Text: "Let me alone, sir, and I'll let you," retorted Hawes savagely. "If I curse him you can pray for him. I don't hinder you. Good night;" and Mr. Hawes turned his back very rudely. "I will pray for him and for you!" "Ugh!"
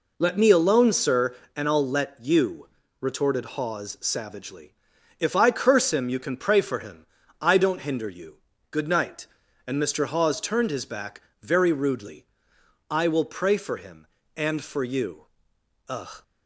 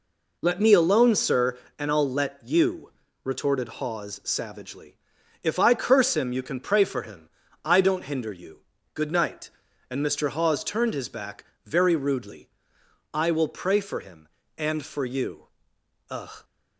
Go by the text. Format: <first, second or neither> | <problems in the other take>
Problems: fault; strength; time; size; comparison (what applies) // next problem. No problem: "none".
neither | pauses between "back" and "very"; slight; the same in both